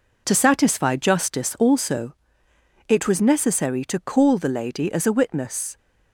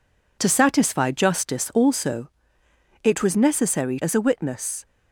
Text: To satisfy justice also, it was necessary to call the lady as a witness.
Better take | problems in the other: first | skips "to call the lady"; at 3.9 s

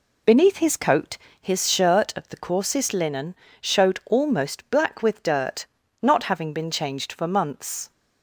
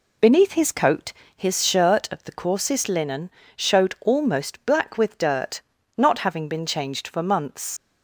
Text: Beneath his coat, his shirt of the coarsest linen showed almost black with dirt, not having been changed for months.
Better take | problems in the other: first | pauses between "linen" and "showed"; slight; at 3.2 s; 0.26 s long; slight in the first // leaves "months" unfinished; at 7.7 s; 90 ms

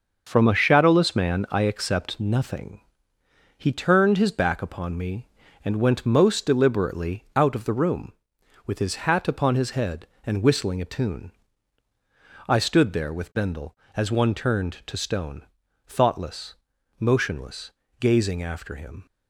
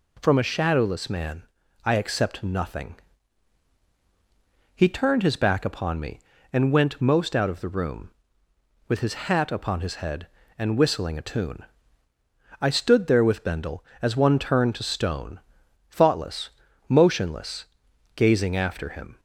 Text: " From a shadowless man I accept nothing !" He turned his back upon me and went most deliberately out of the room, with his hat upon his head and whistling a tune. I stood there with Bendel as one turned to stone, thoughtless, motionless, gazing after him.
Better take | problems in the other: first | pauses between "man" and "I"; at 1.4 s; 0.40 s long // skips "deliberately"; at 7.3 s // pauses between "his" and "hat"; slight; at 9.1 s; 0.16 s long

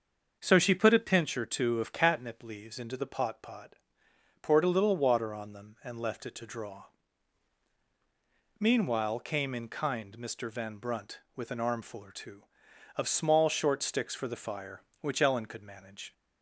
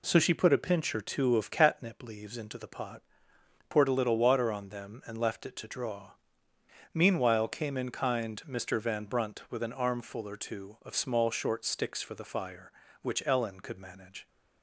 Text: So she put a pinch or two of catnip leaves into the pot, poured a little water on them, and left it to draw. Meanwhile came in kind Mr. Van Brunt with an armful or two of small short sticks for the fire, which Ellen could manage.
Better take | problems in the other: second | starts louder than the rest; until 1.4 s; 6.5 dB // says "pot" twice; at 3.4 s

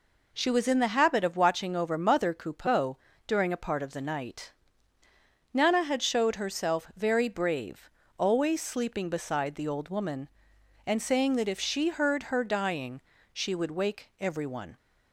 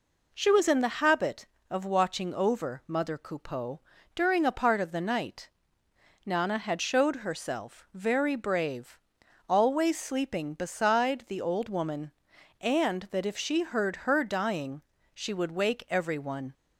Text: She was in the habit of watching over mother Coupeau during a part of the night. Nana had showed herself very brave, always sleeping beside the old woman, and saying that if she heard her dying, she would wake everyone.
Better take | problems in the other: first | pauses between "Coupeau" and "during"; slight; at 3.8 s; 0.34 s long; slight in the first // skips "saying"; at 13.1 s

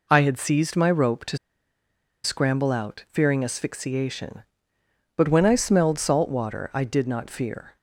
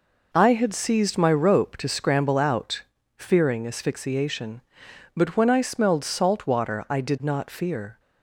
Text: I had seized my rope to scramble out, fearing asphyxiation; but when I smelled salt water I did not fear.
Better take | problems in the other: second | pauses between "to" and "scramble"; noticeable; at 1.3 s; 0.87 s long

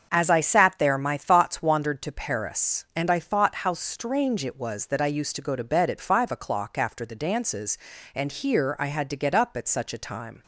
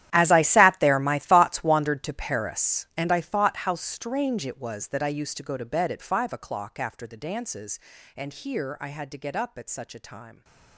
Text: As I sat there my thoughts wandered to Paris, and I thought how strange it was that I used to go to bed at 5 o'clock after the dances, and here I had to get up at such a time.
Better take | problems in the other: first | gets quieter; strong; throughout; 18 dB // starts louder than the rest; strong; until 1.1 s; 12 dB; also in the first

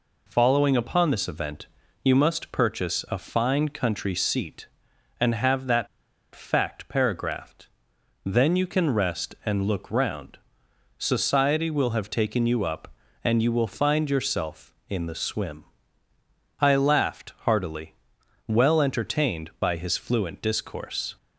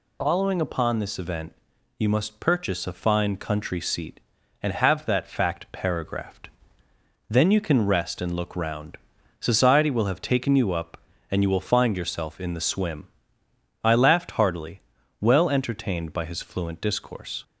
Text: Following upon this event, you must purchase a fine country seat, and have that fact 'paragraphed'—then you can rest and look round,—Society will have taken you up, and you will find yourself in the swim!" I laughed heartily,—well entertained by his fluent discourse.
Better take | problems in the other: second | pauses between "that" and "fact"; noticeable; at 5.8 s; 0.46 s long

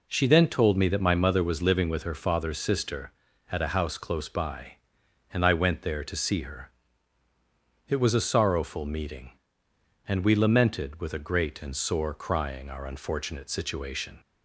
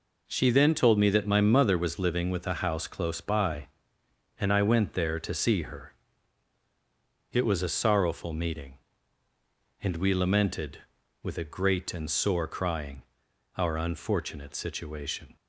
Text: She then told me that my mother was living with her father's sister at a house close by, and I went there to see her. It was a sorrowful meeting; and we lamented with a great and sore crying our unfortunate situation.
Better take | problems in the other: first | skips "her father's sister at"; at 2.4 s // pauses between "crying" and "our"; noticeable; at 13.0 s; 0.54 s long

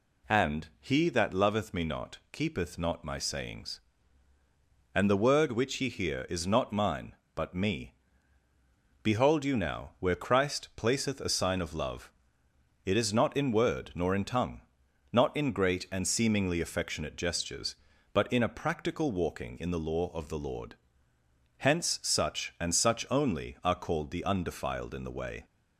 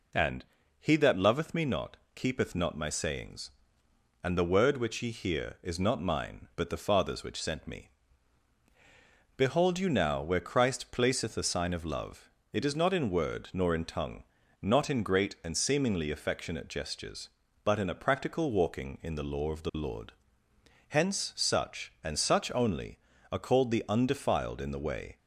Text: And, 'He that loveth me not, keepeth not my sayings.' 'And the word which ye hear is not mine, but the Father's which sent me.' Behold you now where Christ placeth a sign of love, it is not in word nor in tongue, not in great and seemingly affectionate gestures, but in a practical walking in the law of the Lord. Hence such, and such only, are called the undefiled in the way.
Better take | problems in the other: second | skips "the Father's which sent"; at 7.5 s

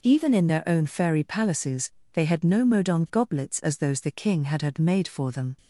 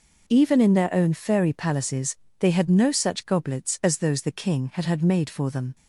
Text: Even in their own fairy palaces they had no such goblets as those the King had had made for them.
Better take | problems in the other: second | pauses between "palaces" and "they"; slight; at 1.9 s; 0.22 s long; slight in the second // says "modon" for "such"; at 2.6 s

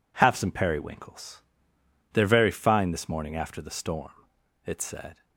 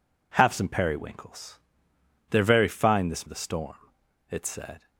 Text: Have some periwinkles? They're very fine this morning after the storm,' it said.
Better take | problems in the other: first | skips "morning after"; at 3.2 s

